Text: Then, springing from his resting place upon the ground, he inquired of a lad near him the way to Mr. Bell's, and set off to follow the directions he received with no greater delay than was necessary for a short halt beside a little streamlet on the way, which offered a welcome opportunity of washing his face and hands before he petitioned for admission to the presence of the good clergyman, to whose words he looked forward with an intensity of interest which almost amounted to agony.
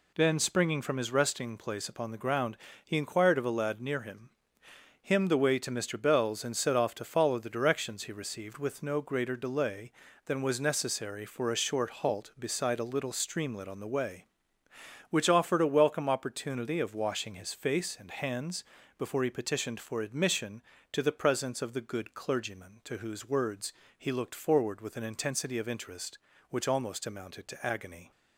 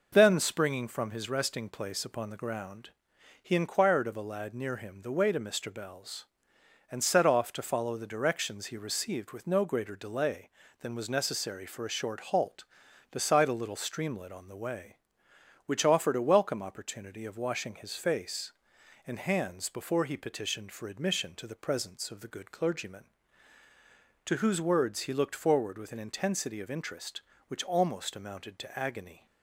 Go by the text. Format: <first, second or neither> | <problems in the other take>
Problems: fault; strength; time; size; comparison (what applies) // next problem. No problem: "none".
second | says "him" twice; at 5.0 s // pauses between "hands" and "before"; slight; at 18.6 s; 0.36 s long // pauses between "words" and "he"; slight; at 23.7 s; 0.24 s long